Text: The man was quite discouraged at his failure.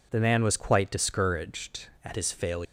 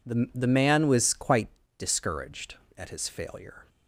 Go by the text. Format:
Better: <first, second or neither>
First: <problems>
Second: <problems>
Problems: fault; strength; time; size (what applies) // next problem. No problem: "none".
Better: first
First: none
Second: says "The" twice; at 0.3 s // pauses between "quite" and "discouraged"; slight; at 1.4 s; 0.30 s long